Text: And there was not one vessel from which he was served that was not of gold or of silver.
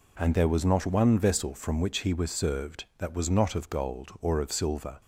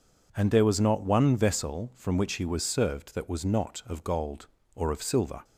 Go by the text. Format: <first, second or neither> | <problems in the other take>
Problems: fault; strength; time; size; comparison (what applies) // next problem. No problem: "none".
neither | none